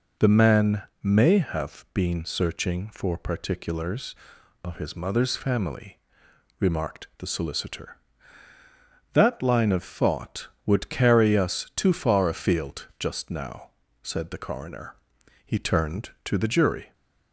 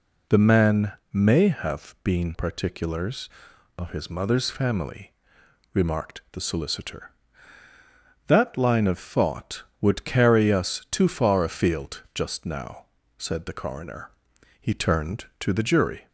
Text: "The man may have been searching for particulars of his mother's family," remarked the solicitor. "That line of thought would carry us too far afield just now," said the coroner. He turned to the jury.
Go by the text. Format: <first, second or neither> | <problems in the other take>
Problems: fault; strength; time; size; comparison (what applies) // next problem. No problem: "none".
first | pauses between "man" and "may"; slight; at 0.9 s; 0.20 s long; slight in the first // skips "searching for"; at 2.3 s